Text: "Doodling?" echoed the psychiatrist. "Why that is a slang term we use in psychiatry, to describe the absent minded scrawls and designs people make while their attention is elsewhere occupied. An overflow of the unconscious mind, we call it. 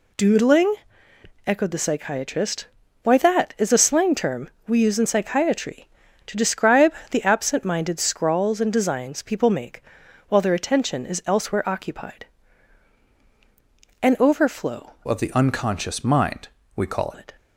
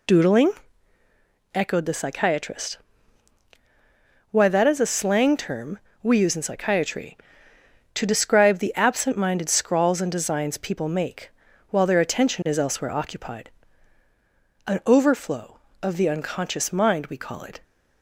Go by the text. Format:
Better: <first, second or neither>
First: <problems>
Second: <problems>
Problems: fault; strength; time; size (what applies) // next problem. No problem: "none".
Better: second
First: pauses between "term" and "we"; slight; at 4.5 s; 0.16 s long // pauses between "describe" and "the"; slight; at 6.9 s; 0.16 s long // pauses between "make" and "while"; noticeable; at 9.8 s; 0.48 s long // changes voice from "of" to "call"; from 15.0 to 17.1 s; 2.1 s long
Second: pauses between "term" and "we"; slight; at 5.7 s; 0.24 s long // pauses between "make" and "while"; at 11.2 s; 0.40 s long